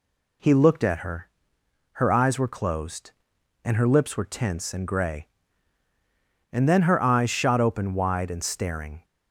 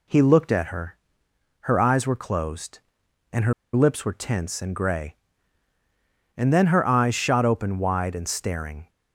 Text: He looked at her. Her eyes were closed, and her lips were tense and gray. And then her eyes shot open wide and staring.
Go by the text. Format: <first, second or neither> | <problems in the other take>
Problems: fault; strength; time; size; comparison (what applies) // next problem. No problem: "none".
first | pauses between "her" and "lips"; slight; at 3.5 s; 0.21 s long